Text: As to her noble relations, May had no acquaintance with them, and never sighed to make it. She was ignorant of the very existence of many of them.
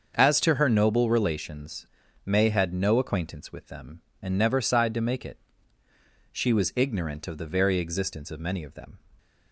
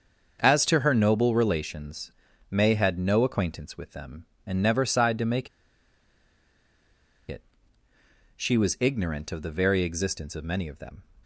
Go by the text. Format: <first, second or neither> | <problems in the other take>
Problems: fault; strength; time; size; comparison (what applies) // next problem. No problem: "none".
first | starts louder than the rest; until 1.4 s; 6.5 dB; also in the first // pauses between "make" and "it"; strong; at 5.4 s; 1.8 s long